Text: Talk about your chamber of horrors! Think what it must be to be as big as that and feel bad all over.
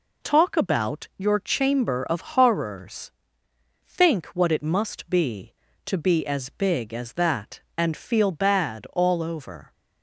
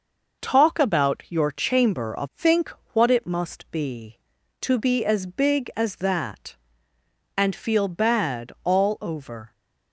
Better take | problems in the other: first | skips "horrors"; at 2.3 s // pauses between "Think" and "what"; slight; at 2.7 s; 0.22 s long

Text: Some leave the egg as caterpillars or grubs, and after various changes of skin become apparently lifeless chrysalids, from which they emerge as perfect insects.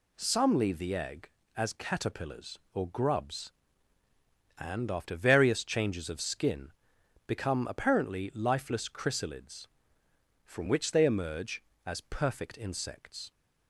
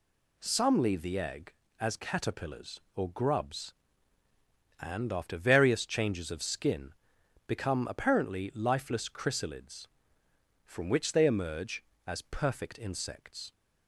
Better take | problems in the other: neither | pauses between "skin" and "become"; noticeable; the same in both

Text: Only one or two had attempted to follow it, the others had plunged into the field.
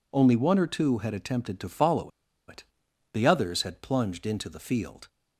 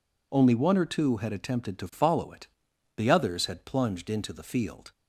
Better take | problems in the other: second | pauses between "follow" and "it"; at 2.1 s; 0.37 s long

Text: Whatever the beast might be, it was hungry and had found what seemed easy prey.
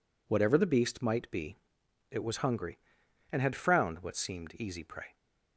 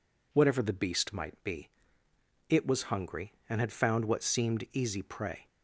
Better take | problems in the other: second | says "frowned" for "found"; at 3.5 s

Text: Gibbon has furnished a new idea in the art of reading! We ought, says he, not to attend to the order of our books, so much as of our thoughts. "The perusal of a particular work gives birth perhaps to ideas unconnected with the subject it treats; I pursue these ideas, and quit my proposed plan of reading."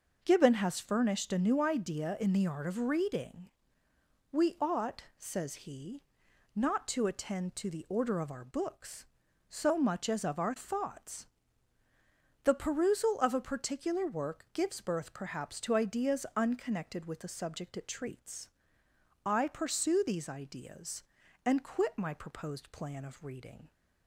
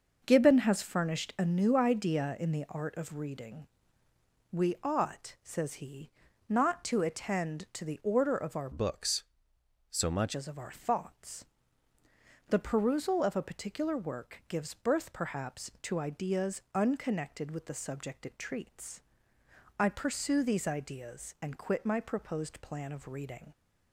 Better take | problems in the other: first | starts louder than the rest; noticeable; until 1.2 s; 6 dB // changes voice from "books" to "much"; from 8.7 to 10.3 s; 1.6 s long

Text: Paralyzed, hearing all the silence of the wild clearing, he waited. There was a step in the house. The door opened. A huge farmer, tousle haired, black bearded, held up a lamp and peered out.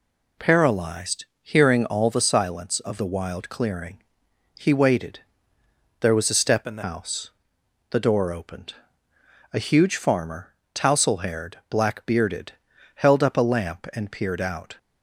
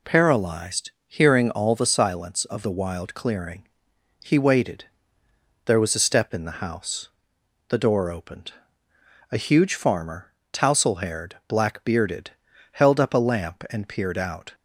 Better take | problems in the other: second | changes voice from "in" to "the"; from 6.6 to 6.8 s; 0.2 s long

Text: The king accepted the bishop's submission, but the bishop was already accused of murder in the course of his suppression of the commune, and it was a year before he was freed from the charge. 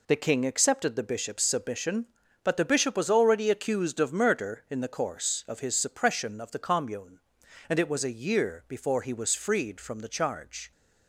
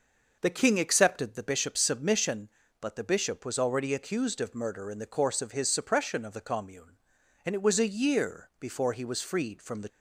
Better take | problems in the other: first | stops before "charge"; at 9.8 s

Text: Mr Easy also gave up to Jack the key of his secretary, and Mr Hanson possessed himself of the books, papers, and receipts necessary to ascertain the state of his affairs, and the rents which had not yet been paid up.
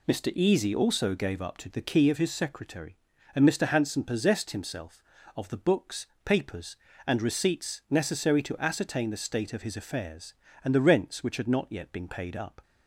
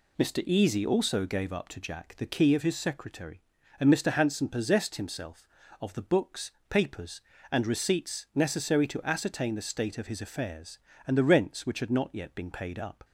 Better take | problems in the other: second | skips "Jack"; at 1.7 s

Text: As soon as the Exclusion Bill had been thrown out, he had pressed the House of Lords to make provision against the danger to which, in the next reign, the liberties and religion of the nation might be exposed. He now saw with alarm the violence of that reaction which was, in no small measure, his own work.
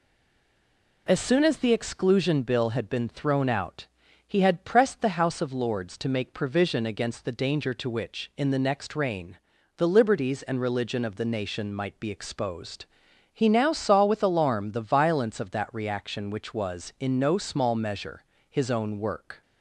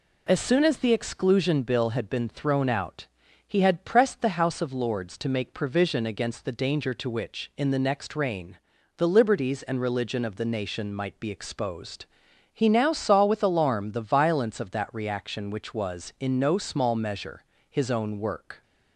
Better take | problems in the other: second | stays silent before the first word; until 1.0 s; 1.0 s long

